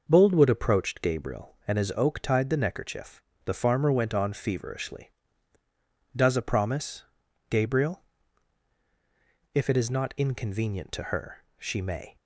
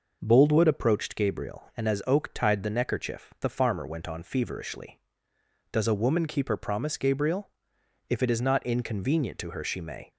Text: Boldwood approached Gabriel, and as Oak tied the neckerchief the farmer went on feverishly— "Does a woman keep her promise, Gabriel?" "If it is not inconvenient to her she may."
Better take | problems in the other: second | pauses between "neckerchief" and "the"; slight; at 3.2 s; 0.22 s long // skips "woman keep her"; at 6.4 s

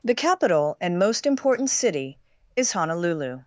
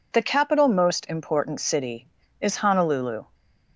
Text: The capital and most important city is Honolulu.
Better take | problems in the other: first | skips "and"; at 0.6 s

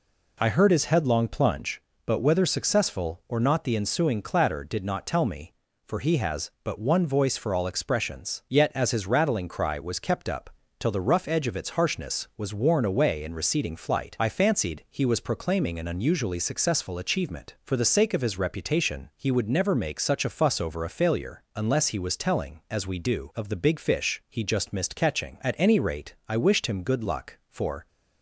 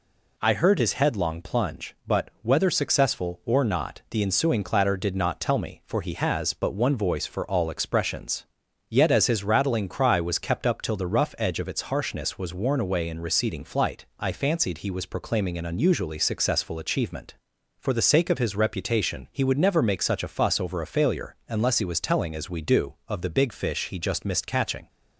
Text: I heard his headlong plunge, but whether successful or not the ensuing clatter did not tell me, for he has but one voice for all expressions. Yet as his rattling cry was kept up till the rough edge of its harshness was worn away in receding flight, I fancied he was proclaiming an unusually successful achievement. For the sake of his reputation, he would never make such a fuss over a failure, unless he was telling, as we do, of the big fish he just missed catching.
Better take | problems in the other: second | pauses between "up" and "till"; slight; at 10.5 s; 0.26 s long // goes on to say "At any rate I wished him good luck for"; strong; from 25.4 s on; 2.4 s long

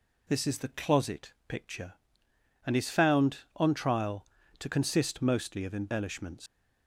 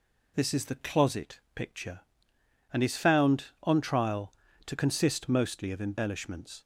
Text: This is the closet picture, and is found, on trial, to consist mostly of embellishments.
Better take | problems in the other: second | pauses between "closet" and "picture"; slight; at 1.3 s; 0.16 s long; slight in the second // leaves "embellishments" unfinished; at 6.4 s; 105 ms

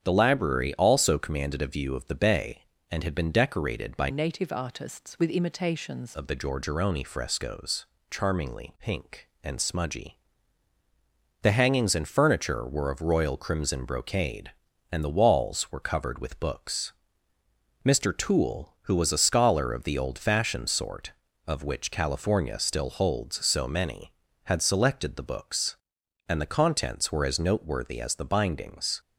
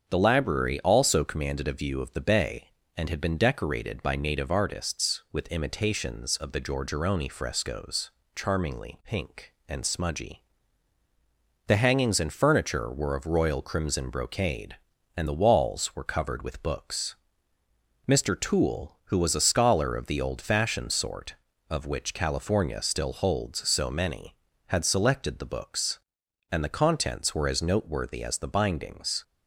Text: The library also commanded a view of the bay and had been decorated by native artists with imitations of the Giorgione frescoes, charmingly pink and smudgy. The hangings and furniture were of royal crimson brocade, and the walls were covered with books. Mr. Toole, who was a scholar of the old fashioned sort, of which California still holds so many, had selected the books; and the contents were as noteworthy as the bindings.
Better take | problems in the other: second | starts louder than the rest; strong; until 1.0 s; 8 dB; also in the second // changes voice from "native" to "imitations"; from 4.1 to 6.1 s; 2.0 s long

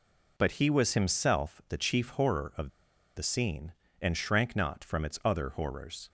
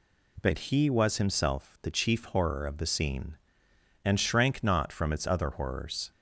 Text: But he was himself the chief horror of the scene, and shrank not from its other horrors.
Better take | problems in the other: second | pauses between "of" and "the"; noticeable; at 2.6 s; 0.47 s long

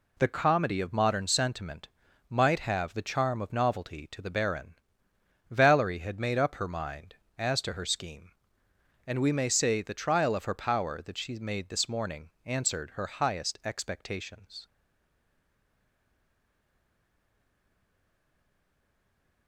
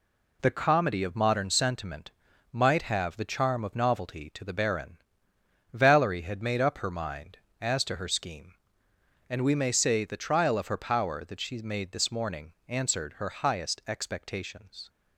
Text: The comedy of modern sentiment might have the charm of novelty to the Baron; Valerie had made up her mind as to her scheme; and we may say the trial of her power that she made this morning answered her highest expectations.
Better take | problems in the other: second | pauses between "sentiment" and "might"; at 1.8 s; 0.40 s long; also in the second // pauses between "morning" and "answered"; slight; at 12.2 s; 0.16 s long; slight in the second // stays silent after the last word; strong; from 14.6 s on; 4.8 s long

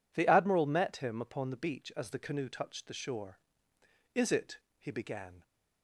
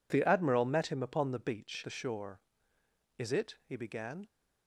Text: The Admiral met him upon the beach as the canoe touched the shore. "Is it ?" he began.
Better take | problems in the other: first | skips "as the canoe touched"; at 1.8 s

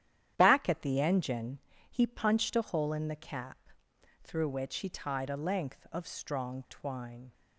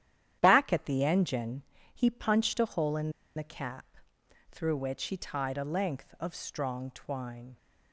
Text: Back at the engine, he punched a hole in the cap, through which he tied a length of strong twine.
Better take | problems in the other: first | starts louder than the rest; strong; until 1.4 s; 10.5 dB; strong in the first // pauses between "in" and "the"; slight; at 3.1 s; 0.25 s long

